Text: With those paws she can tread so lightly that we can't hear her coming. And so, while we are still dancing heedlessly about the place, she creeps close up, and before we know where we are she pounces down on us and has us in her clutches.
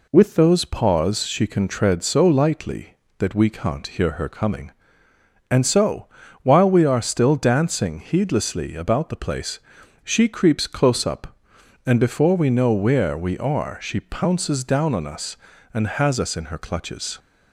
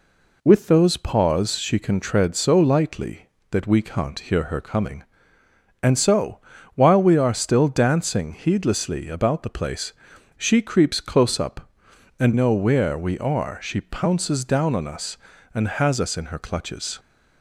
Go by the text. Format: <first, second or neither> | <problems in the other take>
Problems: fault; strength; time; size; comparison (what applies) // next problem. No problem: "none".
first | skips "before we"; at 12.3 s